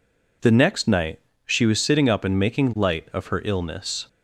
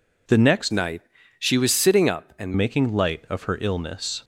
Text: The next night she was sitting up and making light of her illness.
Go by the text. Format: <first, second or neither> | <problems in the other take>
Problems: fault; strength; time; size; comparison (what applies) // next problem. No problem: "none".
first | changes voice from "night" to "and"; from 0.7 to 2.5 s; 1.8 s long // pauses between "night" and "she"; slight; at 1.0 s; 0.36 s long; slight in the first